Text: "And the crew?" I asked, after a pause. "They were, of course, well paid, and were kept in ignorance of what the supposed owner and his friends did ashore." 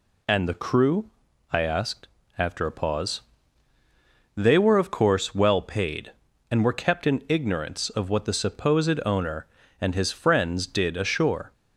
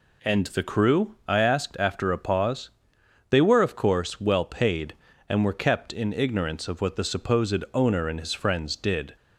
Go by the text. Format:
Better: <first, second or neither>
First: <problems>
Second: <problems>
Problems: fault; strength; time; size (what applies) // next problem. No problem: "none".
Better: first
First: none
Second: stops before "ashore"; at 9.1 s